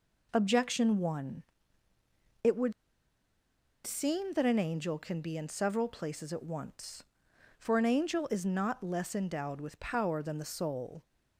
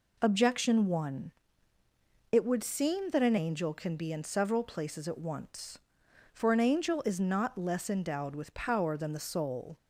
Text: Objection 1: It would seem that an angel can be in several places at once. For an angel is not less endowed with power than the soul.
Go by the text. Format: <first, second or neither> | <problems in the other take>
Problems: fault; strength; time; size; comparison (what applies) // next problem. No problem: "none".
second | pauses between "would" and "seem"; at 2.7 s; 1.1 s long